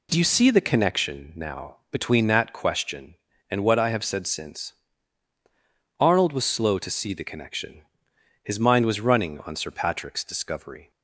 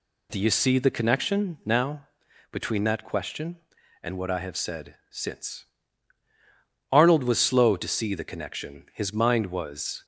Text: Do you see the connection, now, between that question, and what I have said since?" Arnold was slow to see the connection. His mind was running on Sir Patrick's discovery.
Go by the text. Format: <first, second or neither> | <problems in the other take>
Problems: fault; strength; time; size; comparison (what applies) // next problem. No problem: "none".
first | stops before "running on Sir Patrick's discovery"; at 10.0 s